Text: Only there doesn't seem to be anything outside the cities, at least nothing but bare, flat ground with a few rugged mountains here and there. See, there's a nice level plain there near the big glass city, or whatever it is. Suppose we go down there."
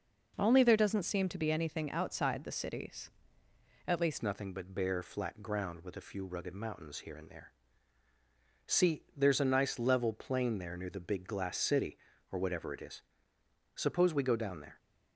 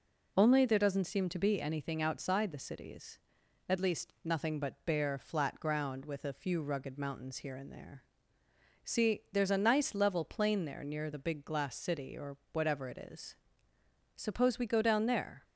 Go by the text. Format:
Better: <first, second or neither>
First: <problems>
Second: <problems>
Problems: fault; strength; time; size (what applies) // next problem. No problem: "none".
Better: second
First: changes voice at "nothing"; from 4.2 s on; 10.5 s long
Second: none